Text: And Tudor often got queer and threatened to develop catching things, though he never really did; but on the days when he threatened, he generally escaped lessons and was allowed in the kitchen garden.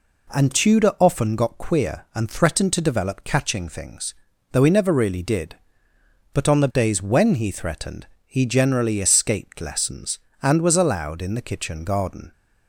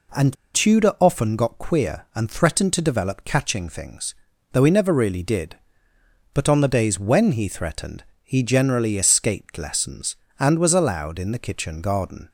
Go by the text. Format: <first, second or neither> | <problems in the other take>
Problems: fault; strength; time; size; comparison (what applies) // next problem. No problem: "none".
first | pauses between "And" and "Tudor"; slight; at 0.3 s; 0.20 s long